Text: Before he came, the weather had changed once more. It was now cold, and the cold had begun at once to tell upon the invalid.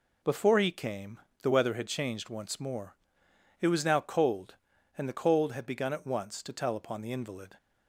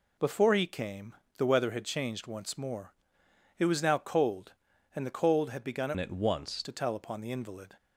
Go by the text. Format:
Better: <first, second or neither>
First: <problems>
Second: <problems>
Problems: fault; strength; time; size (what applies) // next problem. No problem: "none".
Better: first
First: none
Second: changes voice from "at" to "once"; from 5.9 to 6.6 s; 0.7 s long